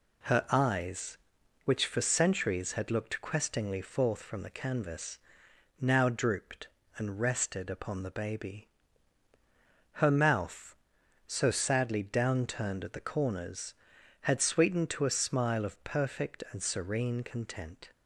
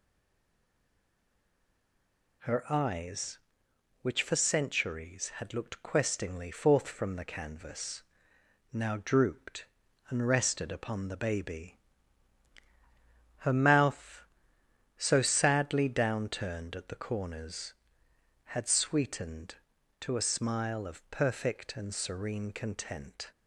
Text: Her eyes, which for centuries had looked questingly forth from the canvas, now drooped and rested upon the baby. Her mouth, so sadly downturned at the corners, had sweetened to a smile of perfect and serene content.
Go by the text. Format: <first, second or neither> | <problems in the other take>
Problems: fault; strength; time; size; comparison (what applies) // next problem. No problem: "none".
first | stays silent before the first word; until 2.4 s; 2.4 s long